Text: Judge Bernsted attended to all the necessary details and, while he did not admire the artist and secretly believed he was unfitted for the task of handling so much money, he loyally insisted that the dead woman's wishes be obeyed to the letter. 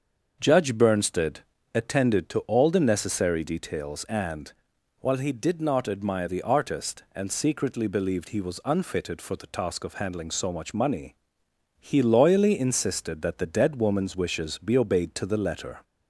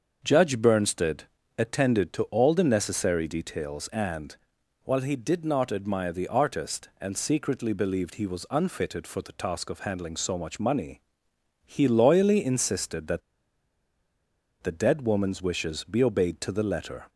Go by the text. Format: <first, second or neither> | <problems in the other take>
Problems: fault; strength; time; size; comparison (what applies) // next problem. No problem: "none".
first | starts louder than the rest; until 1.5 s; 6.5 dB; also in the first // pauses between "Bernsted" and "attended"; slight; at 1.2 s; 0.34 s long; slight in the first // pauses between "that" and "the"; strong; at 13.2 s; 1.4 s long